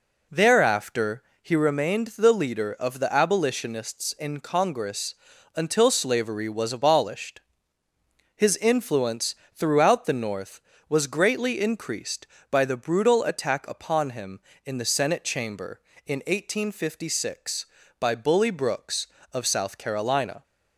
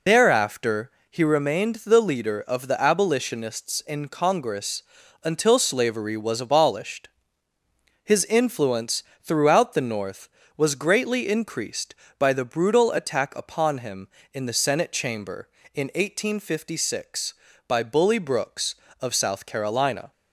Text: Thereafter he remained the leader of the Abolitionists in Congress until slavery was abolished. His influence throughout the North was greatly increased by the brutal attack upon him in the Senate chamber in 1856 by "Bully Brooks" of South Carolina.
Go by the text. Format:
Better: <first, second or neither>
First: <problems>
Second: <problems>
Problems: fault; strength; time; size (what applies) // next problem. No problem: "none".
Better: first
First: pauses between "Thereafter" and "he"; slight; at 1.2 s; 0.18 s long // pauses between "Congress" and "until"; at 5.1 s; 0.40 s long // pauses between "influence" and "throughout"; slight; at 9.3 s; 0.20 s long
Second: loses the start of "Thereafter"; at 0.0 s; 75 ms // pauses between "Thereafter" and "he"; slight; at 0.9 s; 0.18 s long // pauses between "Congress" and "until"; at 4.8 s; 0.40 s long // pauses between "influence" and "throughout"; slight; at 9.0 s; 0.20 s long